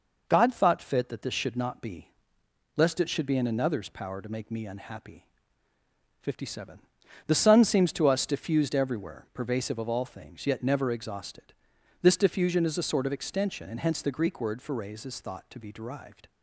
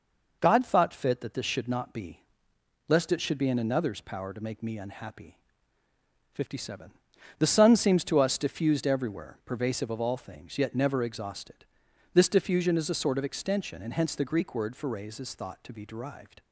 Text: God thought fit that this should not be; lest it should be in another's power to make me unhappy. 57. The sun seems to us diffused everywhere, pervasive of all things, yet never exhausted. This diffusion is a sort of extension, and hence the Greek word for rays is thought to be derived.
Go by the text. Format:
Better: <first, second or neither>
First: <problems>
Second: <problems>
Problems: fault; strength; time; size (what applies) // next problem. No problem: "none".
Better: neither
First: none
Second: none